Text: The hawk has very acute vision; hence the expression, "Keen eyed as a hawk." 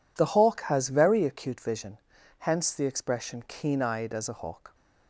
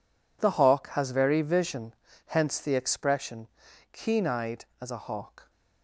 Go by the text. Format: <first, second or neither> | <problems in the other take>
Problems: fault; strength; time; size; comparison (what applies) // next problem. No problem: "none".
first | skips "acute"; at 1.4 s